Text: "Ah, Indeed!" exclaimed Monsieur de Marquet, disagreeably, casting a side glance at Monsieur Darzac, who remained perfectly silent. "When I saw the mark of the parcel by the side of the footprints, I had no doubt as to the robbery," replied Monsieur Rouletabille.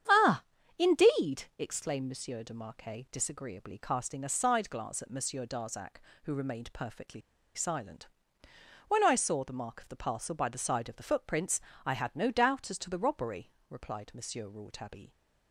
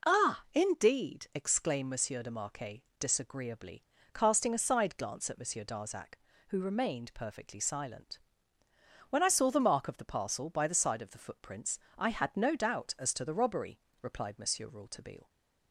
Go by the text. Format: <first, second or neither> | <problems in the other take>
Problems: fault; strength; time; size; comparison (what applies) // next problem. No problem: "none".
second | starts louder than the rest; strong; until 1.4 s; 8.5 dB // pauses between "perfectly" and "silent"; slight; at 7.2 s; 0.34 s long